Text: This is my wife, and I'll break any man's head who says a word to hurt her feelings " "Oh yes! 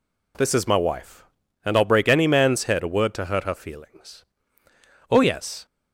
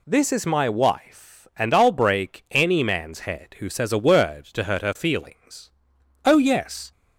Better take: second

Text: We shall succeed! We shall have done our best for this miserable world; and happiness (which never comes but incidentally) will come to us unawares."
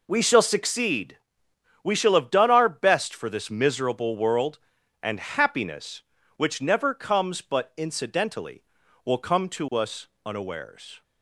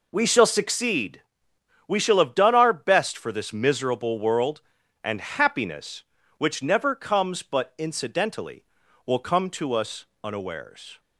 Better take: neither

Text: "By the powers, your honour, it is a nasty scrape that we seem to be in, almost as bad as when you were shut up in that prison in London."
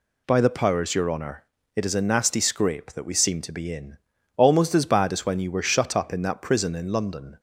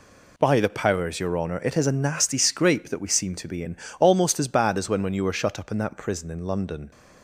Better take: first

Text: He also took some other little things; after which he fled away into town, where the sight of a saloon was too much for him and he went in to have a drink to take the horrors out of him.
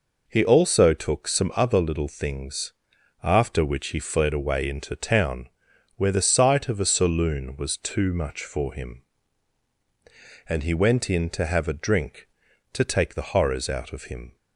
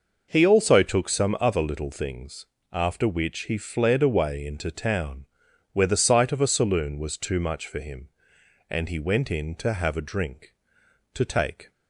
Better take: first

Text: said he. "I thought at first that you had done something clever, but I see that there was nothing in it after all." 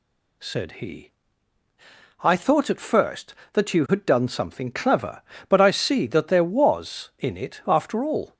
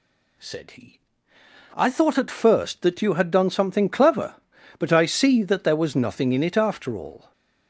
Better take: second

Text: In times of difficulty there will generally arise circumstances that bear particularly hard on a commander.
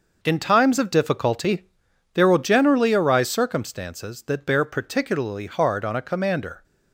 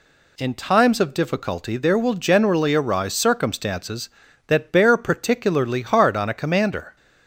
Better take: second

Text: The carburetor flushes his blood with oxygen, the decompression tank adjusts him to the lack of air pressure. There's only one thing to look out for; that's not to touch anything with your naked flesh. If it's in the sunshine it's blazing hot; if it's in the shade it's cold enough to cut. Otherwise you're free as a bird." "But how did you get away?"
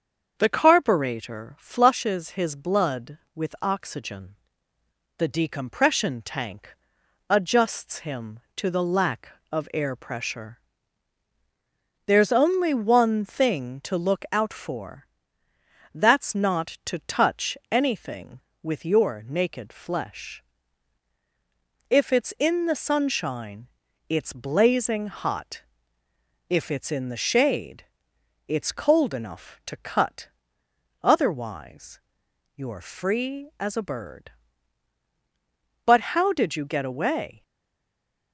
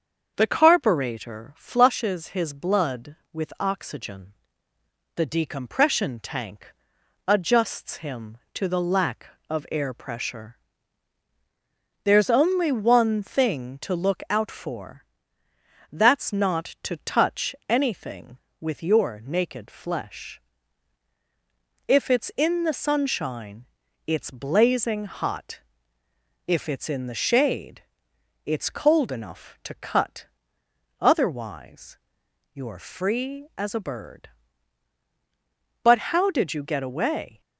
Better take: second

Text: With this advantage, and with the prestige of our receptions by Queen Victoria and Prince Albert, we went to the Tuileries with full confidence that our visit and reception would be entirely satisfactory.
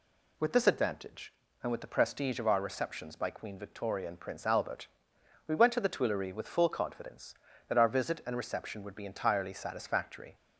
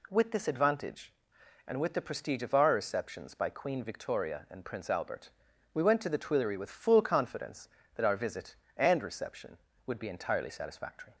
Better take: neither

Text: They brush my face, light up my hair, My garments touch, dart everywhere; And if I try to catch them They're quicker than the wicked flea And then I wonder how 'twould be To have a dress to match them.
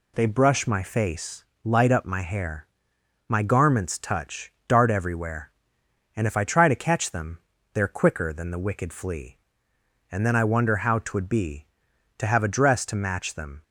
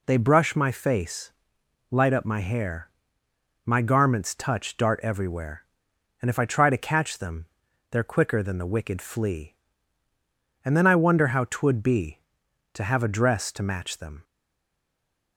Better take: first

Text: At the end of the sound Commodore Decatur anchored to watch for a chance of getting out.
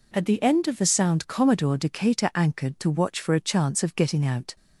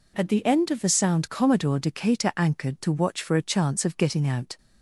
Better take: neither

